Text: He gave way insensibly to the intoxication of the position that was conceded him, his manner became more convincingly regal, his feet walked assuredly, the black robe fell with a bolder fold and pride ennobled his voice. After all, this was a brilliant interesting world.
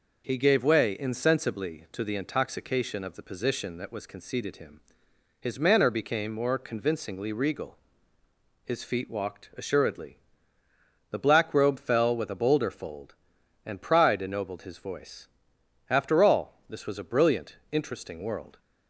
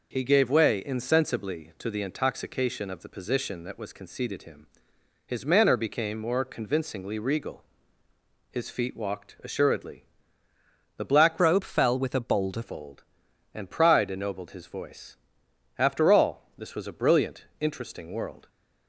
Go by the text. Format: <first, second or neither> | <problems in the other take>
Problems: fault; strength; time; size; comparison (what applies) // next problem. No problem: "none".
first | changes voice from "robe" to "bolder"; from 11.3 to 12.6 s; 1.3 s long